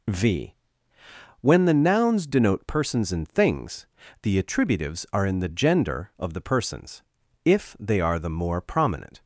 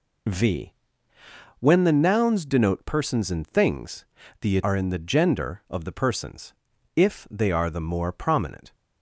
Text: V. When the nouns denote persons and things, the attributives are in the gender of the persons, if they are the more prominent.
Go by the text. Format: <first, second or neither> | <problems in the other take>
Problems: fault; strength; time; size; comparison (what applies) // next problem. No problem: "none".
first | skips "attributives"; at 4.6 s